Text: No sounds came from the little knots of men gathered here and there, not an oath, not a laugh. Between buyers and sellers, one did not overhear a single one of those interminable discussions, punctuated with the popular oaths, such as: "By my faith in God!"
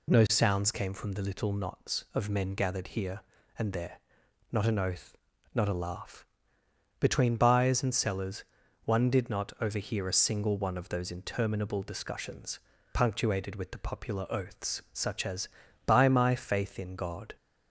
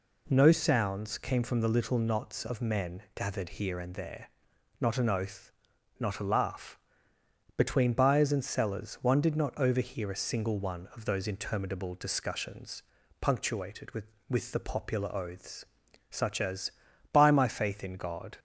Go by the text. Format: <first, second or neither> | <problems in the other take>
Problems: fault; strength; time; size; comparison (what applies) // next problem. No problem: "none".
first | says "with" twice; at 14.2 s